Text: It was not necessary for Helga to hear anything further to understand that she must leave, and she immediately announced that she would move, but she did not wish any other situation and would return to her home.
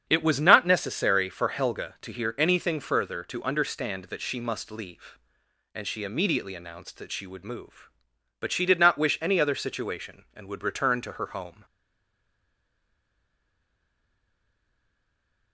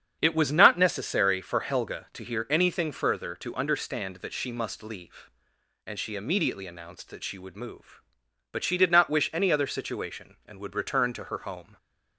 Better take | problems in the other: second | starts louder than the rest; strong; until 1.0 s; 8 dB; strong in the second // stays silent after the last word; strong; from 11.6 s on; 3.9 s long

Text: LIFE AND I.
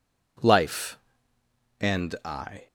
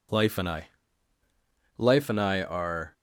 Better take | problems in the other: first | goes on to say "Life and I are"; noticeable; from 1.7 s on; 1.1 s long

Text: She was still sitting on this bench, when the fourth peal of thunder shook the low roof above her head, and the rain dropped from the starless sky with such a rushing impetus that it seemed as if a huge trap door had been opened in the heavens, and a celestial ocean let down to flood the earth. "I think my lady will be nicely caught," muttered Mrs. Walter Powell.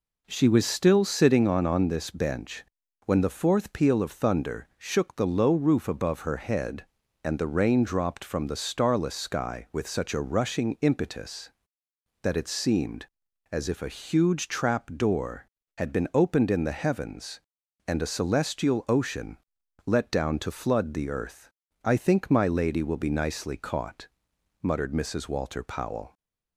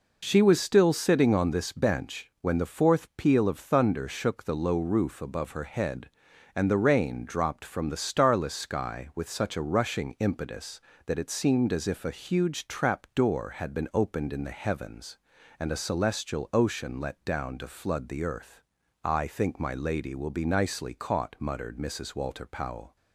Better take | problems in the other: second | says "on" twice; at 1.6 s // pauses between "ocean" and "let"; noticeable; at 19.3 s; 0.50 s long

